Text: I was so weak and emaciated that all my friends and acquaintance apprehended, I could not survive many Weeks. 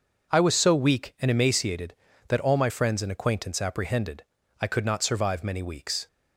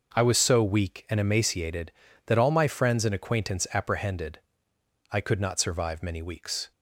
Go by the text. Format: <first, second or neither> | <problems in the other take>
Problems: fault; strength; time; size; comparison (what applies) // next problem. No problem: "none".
neither | none